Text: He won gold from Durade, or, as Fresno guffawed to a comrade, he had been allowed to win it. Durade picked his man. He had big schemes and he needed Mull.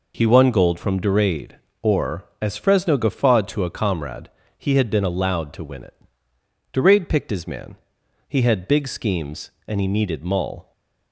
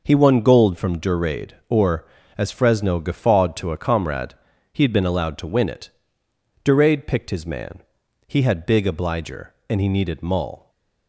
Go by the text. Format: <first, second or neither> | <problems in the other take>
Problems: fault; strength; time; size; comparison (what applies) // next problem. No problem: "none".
first | says "obliger" for "schemes"; at 8.8 s // stays silent after the last word; slight; from 10.5 s on; 0.5 s long